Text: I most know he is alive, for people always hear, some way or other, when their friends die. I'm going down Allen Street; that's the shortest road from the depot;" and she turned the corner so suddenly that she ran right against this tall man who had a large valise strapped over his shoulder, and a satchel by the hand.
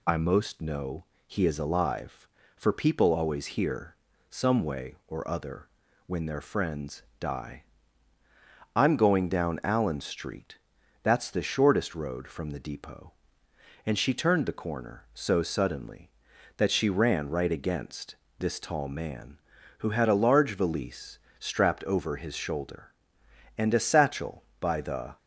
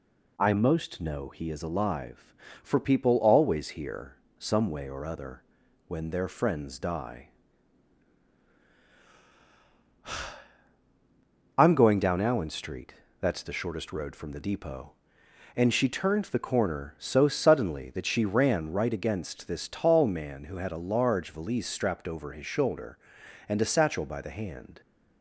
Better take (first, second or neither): second